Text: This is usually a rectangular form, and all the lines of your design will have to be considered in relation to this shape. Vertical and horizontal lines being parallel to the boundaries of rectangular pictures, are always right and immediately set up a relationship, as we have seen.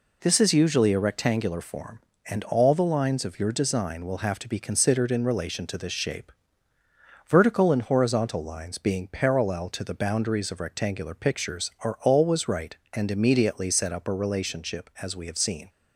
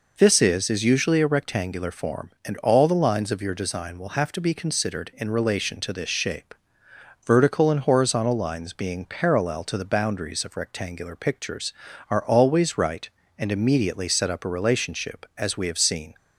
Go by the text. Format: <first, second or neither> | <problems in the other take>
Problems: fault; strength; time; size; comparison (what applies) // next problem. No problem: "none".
first | says "is" twice; at 0.6 s